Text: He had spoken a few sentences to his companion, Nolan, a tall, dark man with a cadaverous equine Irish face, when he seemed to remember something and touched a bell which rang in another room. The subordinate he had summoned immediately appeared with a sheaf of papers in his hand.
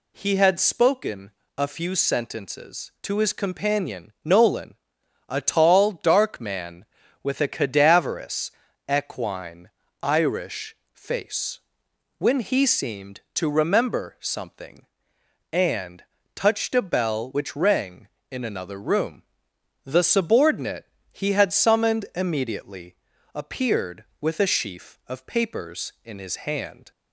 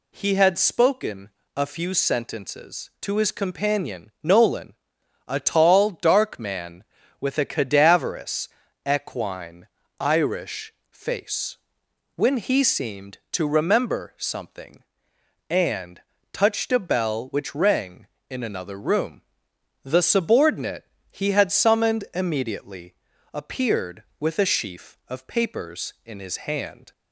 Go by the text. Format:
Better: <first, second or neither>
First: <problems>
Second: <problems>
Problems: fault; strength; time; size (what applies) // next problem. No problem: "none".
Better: neither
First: pauses between "spoken" and "a"; slight; at 1.3 s; 0.26 s long // pauses between "cadaverous" and "equine"; slight; at 8.5 s; 0.36 s long // pauses between "equine" and "Irish"; slight; at 9.6 s; 0.34 s long // pauses between "Irish" and "face"; slight; at 10.7 s; 0.16 s long // pauses between "and" and "touched"; slight; at 16.0 s; 0.32 s long // pauses between "subordinate" and "he"; slight; at 20.8 s; 0.26 s long // pauses between "immediately" and "appeared"; at 22.9 s; 0.38 s long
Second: pauses between "spoken" and "a"; slight; at 1.3 s; 0.26 s long // pauses between "cadaverous" and "equine"; slight; at 8.4 s; 0.36 s long // pauses between "equine" and "Irish"; slight; at 9.6 s; 0.34 s long // pauses between "Irish" and "face"; slight; at 10.7 s; 0.16 s long // pauses between "and" and "touched"; slight; at 16.0 s; 0.32 s long // pauses between "subordinate" and "he"; slight; at 20.8 s; 0.26 s long // pauses between "immediately" and "appeared"; at 22.9 s; 0.38 s long